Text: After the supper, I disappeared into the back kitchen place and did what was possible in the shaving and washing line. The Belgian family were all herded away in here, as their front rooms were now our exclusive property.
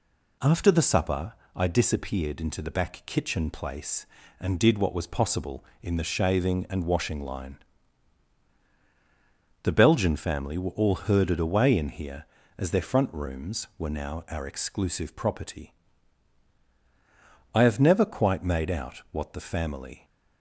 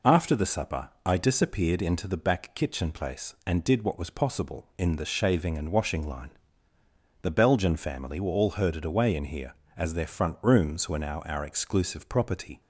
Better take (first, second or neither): second